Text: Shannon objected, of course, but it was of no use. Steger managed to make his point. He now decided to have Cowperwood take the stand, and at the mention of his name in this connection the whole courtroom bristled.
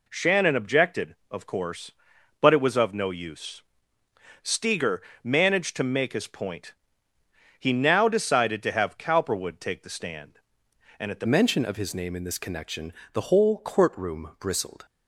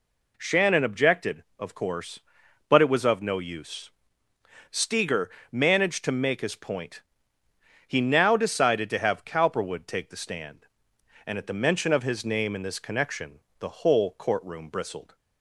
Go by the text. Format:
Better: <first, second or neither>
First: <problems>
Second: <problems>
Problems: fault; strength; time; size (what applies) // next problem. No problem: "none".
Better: second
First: pauses between "Steger" and "managed"; slight; at 5.0 s; 0.22 s long // changes voice at "mention"; from 11.2 s on; 3.6 s long // pauses between "connection" and "the"; slight; at 12.9 s; 0.20 s long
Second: pauses between "Steger" and "managed"; slight; at 5.3 s; 0.22 s long // pauses between "connection" and "the"; slight; at 13.3 s; 0.20 s long